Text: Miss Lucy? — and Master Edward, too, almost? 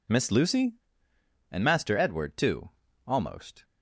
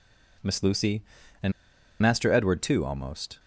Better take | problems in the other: first | pauses between "and" and "Master"; noticeable; at 1.5 s; 0.49 s long

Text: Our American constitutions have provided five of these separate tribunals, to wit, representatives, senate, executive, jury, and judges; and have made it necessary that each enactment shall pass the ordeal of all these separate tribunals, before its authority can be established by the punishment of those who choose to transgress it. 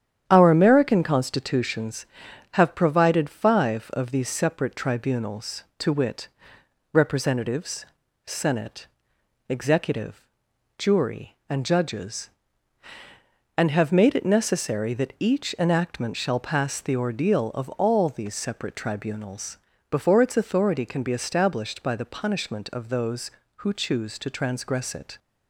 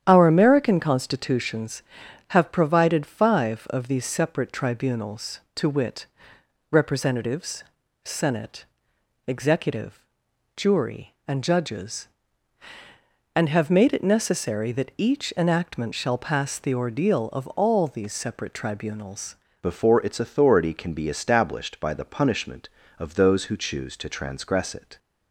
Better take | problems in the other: first | starts louder than the rest; strong; until 1.0 s; 9.5 dB; strong in the first // changes voice at "before"; from 19.6 s on; 5.3 s long

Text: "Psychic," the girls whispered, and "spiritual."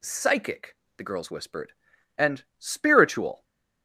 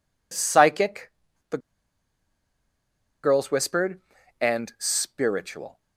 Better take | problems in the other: first | pauses between "the" and "girls"; strong; at 1.5 s; 1.6 s long

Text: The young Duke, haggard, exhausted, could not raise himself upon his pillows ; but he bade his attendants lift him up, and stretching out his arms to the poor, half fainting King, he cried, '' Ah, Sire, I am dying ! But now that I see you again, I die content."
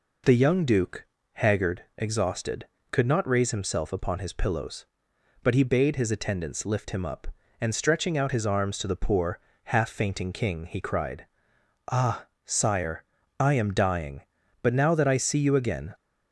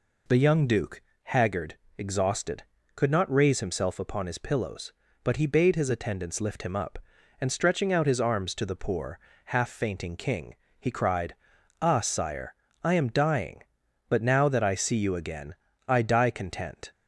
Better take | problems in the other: second | stops before "I die content"; at 15.9 s

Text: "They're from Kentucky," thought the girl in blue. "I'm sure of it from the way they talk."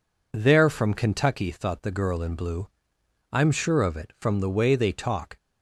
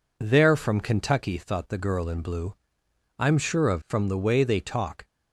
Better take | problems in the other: first | skips "it"; at 3.8 s

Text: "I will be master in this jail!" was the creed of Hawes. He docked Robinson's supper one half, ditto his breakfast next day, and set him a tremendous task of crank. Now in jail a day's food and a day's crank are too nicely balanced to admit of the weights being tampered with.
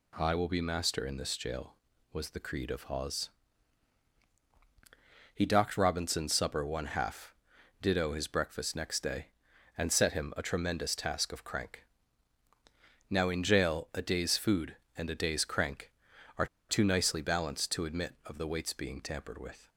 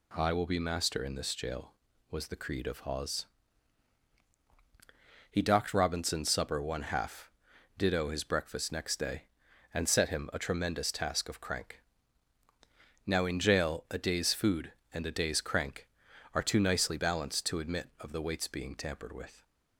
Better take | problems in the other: second | pauses between "are" and "too"; slight; at 16.4 s; 0.23 s long

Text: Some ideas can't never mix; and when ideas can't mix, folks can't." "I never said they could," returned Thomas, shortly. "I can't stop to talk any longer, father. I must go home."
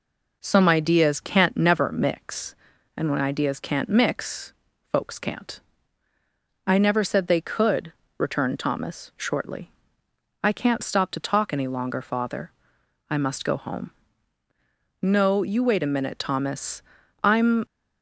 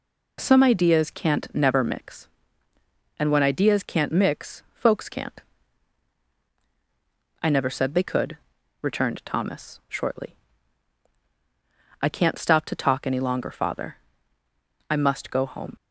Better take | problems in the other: second | goes on to say "No you wait a minute Thomas I'm"; strong; from 15.0 s on; 2.6 s long

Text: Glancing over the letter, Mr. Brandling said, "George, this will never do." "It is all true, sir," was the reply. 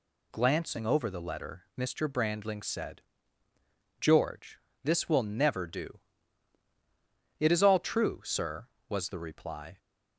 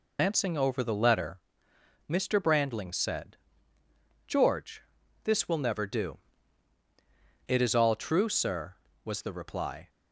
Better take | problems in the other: first | loses the start of "Glancing"; at 0.1 s; 140 ms

